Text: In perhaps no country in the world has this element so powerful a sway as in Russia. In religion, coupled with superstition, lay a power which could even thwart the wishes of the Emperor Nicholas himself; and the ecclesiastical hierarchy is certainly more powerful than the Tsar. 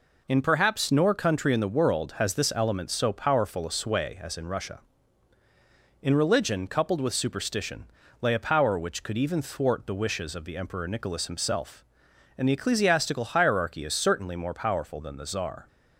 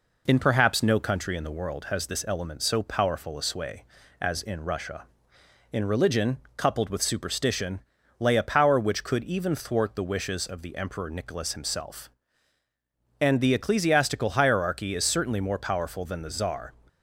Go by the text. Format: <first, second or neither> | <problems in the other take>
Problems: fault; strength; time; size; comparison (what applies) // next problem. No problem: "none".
second | says "nor" for "no"; at 0.8 s